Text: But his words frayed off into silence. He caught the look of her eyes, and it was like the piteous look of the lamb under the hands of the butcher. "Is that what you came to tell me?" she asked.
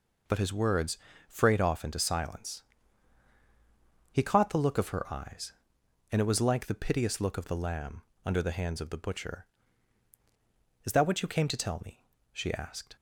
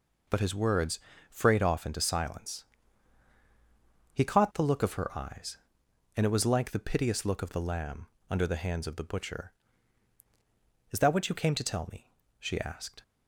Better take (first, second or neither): neither